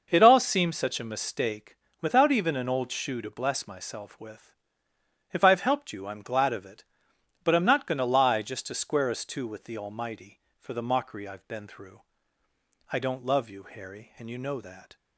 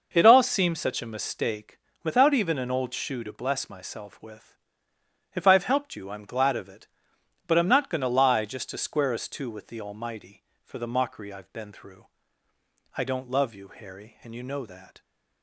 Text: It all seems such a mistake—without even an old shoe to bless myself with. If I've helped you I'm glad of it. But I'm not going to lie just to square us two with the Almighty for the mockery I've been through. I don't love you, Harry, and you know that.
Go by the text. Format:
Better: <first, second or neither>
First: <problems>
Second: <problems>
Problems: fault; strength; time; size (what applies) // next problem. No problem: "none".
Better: neither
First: none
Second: none